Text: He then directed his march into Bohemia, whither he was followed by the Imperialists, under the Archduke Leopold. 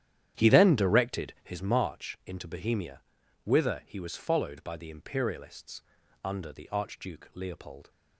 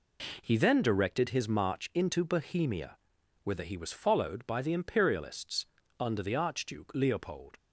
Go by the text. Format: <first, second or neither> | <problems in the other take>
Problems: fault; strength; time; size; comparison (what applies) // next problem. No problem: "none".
second | starts louder than the rest; strong; until 1.6 s; 10.5 dB